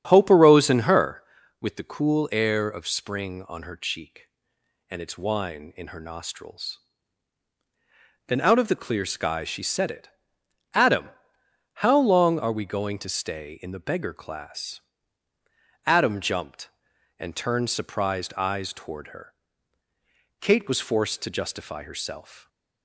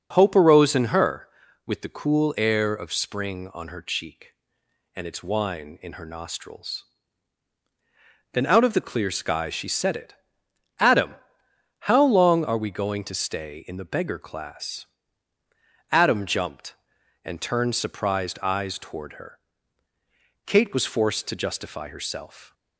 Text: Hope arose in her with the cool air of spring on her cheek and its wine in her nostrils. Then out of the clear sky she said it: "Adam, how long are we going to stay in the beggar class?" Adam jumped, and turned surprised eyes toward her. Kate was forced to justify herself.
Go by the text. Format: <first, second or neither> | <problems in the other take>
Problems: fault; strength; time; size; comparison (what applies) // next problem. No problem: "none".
second | starts louder than the rest; strong; until 1.4 s; 8 dB